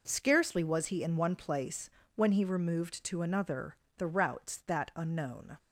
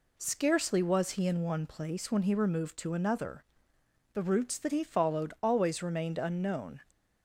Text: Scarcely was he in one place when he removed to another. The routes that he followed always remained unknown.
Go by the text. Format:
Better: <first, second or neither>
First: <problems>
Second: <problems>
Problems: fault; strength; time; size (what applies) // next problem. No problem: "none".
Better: second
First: pauses between "place" and "when"; slight; at 1.9 s; 0.24 s long // skips "he followed always remained"; at 4.9 s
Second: none